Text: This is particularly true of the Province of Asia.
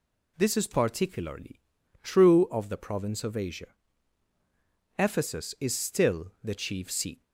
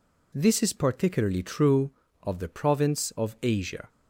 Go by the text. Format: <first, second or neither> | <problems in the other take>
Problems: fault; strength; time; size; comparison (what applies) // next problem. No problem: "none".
second | pauses between "particularly" and "true"; at 1.5 s; 0.42 s long // goes on to say "Ephesus is still the chief seat"; strong; from 4.9 s on; 2.2 s long